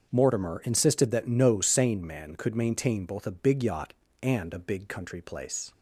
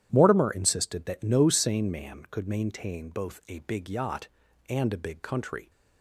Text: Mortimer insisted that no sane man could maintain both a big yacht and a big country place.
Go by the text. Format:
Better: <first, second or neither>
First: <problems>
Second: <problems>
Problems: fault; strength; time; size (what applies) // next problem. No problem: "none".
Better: first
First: starts louder than the rest; until 1.1 s; 7 dB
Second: starts louder than the rest; strong; until 1.1 s; 10.5 dB // stops before "place"; at 5.6 s